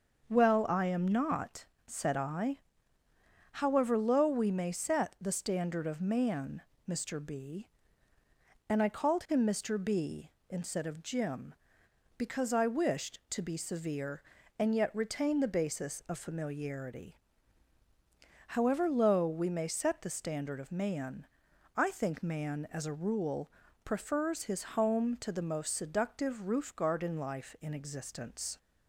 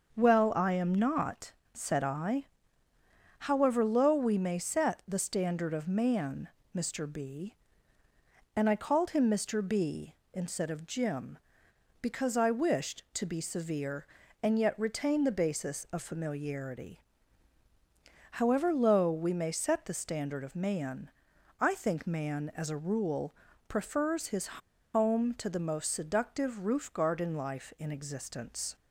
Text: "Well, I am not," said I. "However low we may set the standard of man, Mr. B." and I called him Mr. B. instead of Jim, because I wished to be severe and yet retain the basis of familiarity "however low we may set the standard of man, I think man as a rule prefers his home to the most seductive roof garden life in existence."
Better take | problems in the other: first | starts louder than the rest; until 1.2 s; 6.5 dB; also in the first // pauses between "familiarity" and "however"; strong; at 16.9 s; 1.3 s long; strong in the first // pauses between "rule" and "prefers"; slight; at 23.3 s; 0.36 s long; slight in the first // pauses between "his" and "home"; noticeable; at 24.4 s; 0.46 s long

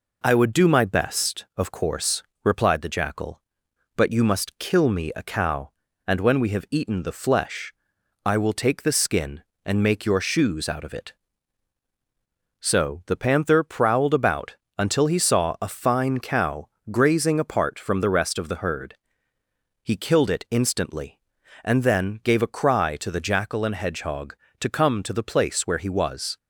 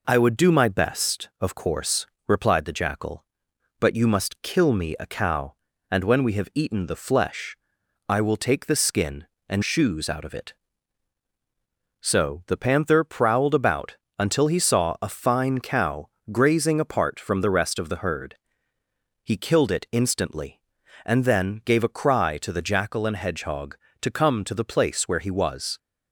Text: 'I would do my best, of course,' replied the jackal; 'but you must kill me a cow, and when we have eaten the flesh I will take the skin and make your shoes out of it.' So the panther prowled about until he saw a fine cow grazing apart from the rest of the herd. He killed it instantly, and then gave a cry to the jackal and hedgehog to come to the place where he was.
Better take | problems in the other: first | pauses between "flesh" and "I"; noticeable; at 7.5 s; 0.50 s long; noticeable in the first // skips "make your"; at 9.6 s // pauses between "about" and "until"; slight; at 13.9 s; 0.22 s long; slight in the first // pauses between "cow" and "grazing"; slight; at 16.0 s; 0.24 s long; slight in the first

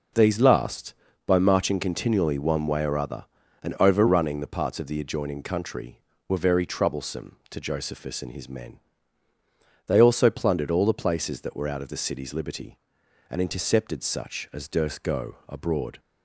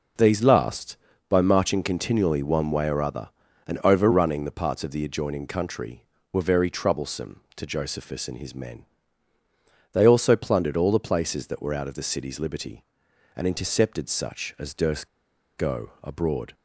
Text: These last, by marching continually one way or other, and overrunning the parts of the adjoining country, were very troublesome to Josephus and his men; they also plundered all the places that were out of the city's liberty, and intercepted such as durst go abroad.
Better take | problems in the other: first | pauses between "durst" and "go"; noticeable; at 15.0 s; 0.49 s long

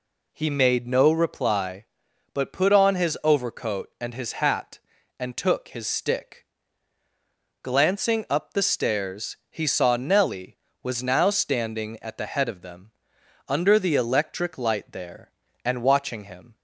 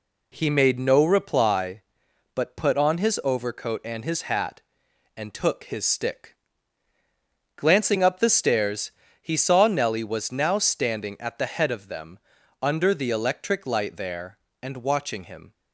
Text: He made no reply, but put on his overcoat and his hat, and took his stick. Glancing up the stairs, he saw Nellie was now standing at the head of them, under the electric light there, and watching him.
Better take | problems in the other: neither | none

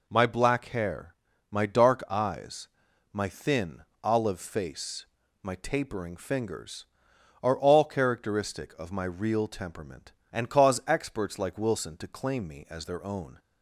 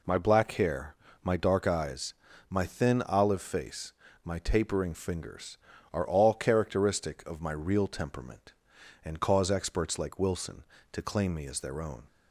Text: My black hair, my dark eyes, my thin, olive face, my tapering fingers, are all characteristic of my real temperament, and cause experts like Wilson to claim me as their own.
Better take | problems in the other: neither | none

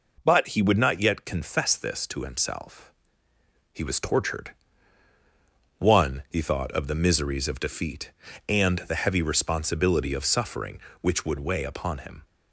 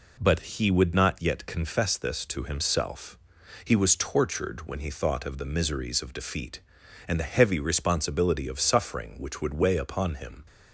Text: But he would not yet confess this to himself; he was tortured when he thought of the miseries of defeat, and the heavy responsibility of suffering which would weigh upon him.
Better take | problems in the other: second | says "one" for "when"; at 5.7 s

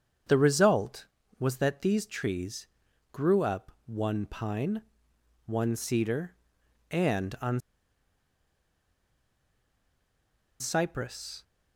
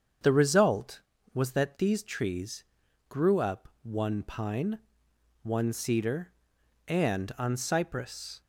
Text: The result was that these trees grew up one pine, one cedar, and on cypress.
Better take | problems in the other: second | starts louder than the rest; strong; until 1.6 s; 7.5 dB; strong in the second // pauses between "trees" and "grew"; noticeable; at 2.6 s; 0.46 s long; noticeable in the second // pauses between "on" and "cypress"; strong; at 7.5 s; 3.0 s long

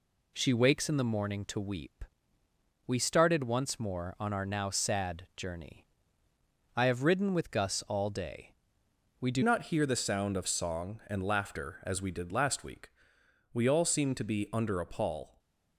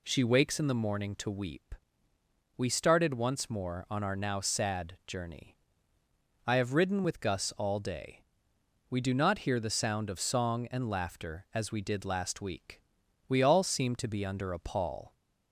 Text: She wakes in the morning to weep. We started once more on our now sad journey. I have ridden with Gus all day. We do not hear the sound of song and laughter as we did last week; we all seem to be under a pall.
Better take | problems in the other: second | changes voice at "not"; from 9.4 s on; 5.4 s long // stays silent after the last word; slight; from 15.2 s on; 0.5 s long

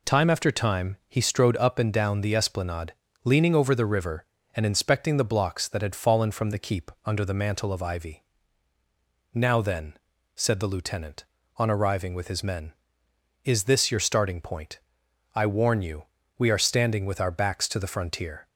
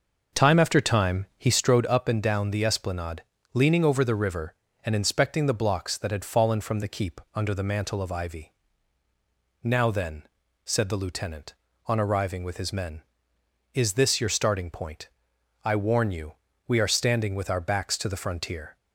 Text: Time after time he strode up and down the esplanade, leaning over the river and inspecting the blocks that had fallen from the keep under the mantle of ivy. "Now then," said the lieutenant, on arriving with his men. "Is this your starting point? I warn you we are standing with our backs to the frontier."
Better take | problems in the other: first | starts louder than the rest; noticeable; until 1.8 s; 6 dB // pauses between "you" and "we"; slight; at 16.3 s; 0.32 s long; slight in the first

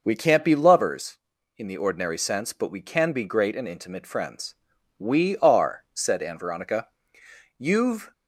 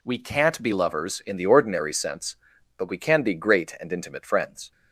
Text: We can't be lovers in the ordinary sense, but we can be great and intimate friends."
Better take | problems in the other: second | goes on to say "We are said Ann Veronica You've"; strong; from 4.9 s on; 3.1 s long

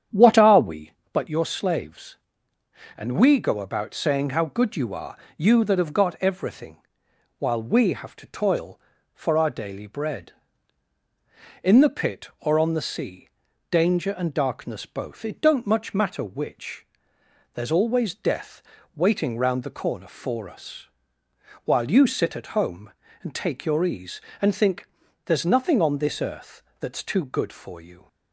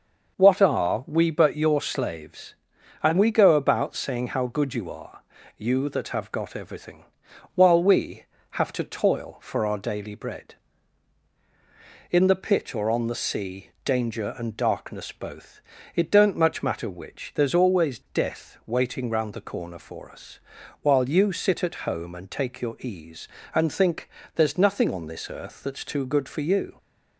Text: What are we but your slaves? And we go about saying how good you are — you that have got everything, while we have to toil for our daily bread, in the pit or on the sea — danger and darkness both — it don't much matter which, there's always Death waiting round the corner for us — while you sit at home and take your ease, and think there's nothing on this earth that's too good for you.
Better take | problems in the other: second | starts louder than the rest; strong; until 1.2 s; 9 dB // pauses between "Death" and "waiting"; slight; at 18.6 s; 0.34 s long // pauses between "think" and "there's"; at 24.8 s; 0.38 s long; slight in the second // pauses between "earth" and "that's"; slight; at 26.6 s; 0.16 s long

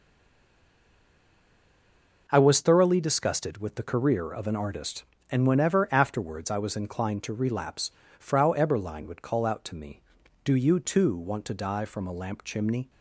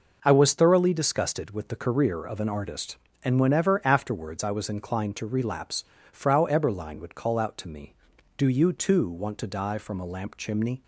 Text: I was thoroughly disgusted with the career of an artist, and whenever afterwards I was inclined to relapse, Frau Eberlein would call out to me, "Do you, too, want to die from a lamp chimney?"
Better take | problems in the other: second | stays silent before the first word; until 2.2 s; 2.2 s long

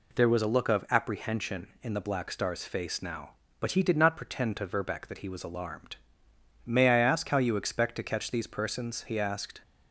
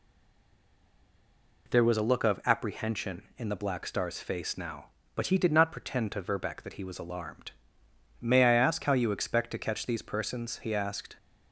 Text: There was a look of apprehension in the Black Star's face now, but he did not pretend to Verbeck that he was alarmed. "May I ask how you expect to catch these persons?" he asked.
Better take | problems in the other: first | stays silent before the first word; noticeable; until 1.6 s; 1.6 s long

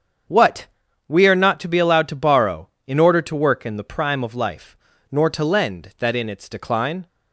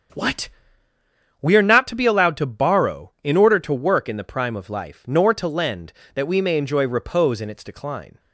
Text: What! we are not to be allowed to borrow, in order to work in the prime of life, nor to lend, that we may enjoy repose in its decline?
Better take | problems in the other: second | starts louder than the rest; until 1.7 s; 7 dB; also in the second // skips "we may enjoy repose"; at 6.1 s

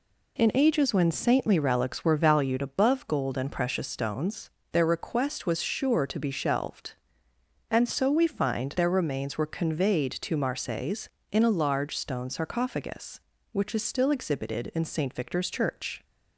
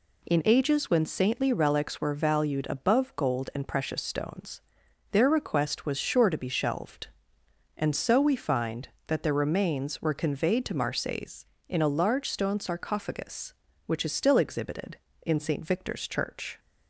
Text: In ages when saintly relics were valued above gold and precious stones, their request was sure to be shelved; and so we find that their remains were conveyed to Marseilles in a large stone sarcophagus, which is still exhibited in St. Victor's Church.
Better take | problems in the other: second | skips "that"; at 8.7 s

